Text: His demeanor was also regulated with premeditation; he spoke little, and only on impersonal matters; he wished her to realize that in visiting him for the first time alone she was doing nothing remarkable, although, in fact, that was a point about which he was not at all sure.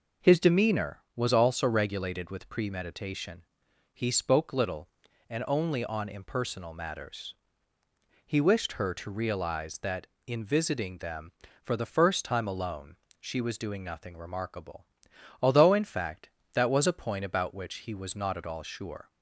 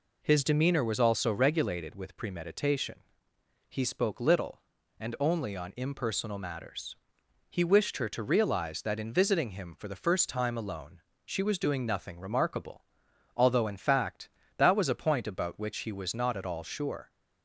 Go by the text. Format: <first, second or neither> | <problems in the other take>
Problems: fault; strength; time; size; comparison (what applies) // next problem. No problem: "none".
second | says "them" for "him"; at 10.9 s // pauses between "alone" and "she"; slight; at 12.9 s; 0.22 s long; slight in the second